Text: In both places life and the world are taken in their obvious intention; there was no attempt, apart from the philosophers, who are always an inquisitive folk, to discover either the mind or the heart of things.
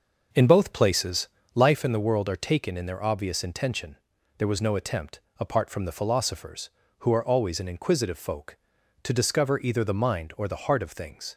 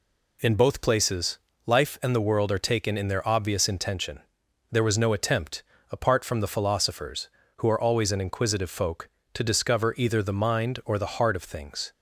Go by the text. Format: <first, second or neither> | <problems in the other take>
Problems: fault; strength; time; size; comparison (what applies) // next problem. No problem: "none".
second | starts louder than the rest; noticeable; until 1.9 s; 6 dB // pauses between "places" and "life"; slight; at 1.2 s; 0.28 s long; slight in the second